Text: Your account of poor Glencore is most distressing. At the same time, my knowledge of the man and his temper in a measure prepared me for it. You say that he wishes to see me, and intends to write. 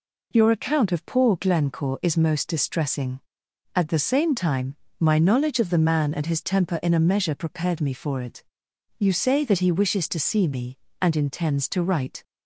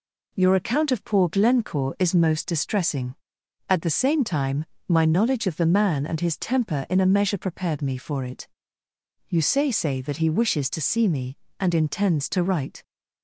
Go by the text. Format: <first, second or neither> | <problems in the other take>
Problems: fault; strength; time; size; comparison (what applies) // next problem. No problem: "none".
first | says "say" twice; at 9.7 s